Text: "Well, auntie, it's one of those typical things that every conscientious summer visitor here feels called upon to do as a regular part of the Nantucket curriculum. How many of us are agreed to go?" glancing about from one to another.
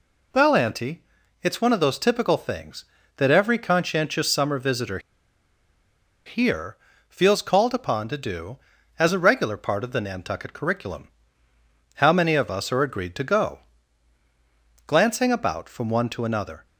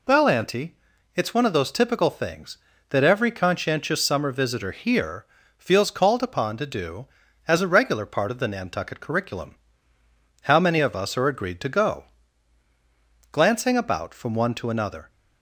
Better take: second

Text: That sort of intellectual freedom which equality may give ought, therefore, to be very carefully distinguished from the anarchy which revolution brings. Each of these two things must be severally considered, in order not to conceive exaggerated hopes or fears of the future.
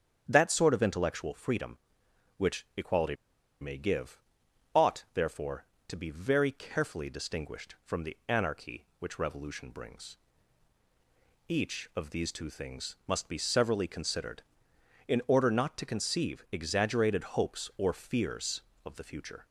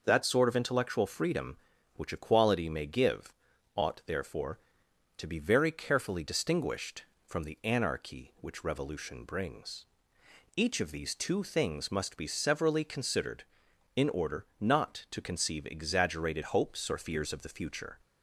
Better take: second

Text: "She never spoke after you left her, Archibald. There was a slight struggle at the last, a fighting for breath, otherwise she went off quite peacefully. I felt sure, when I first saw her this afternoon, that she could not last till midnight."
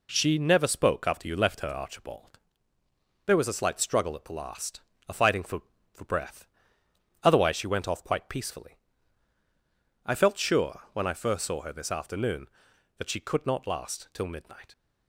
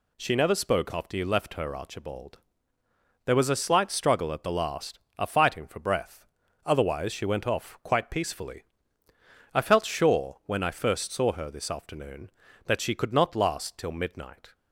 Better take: second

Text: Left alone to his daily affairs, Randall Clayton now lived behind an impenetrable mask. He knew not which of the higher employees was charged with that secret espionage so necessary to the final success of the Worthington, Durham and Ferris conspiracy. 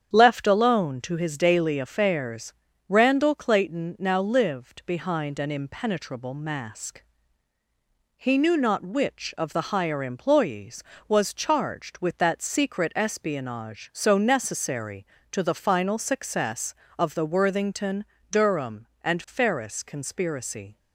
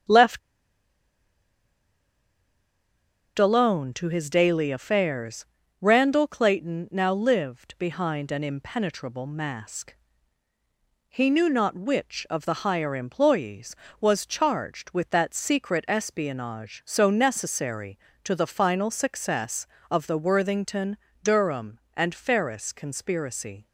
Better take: first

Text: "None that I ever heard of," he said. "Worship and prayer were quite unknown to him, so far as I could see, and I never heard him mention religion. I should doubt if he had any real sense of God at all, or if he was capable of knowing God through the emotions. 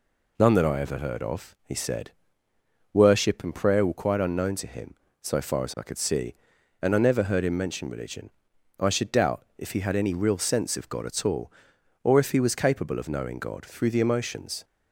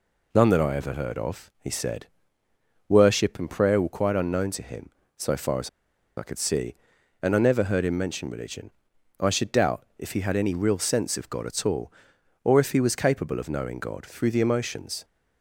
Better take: first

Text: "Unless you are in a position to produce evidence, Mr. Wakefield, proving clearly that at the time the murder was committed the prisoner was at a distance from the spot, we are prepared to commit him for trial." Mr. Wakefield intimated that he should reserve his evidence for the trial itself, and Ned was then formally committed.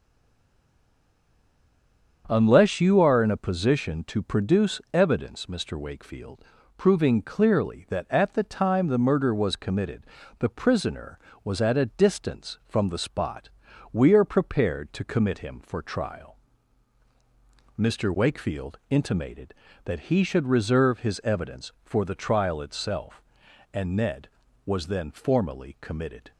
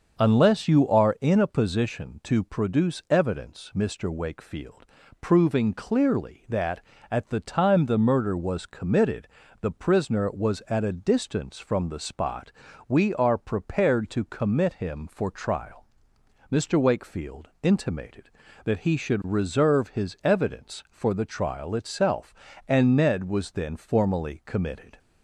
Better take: second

